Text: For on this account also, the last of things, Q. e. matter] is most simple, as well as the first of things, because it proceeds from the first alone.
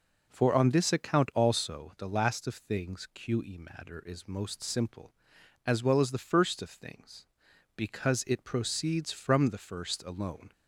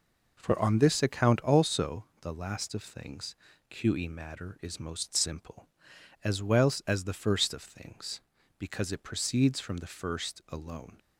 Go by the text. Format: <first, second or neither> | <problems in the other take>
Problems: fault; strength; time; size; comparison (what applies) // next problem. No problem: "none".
neither | none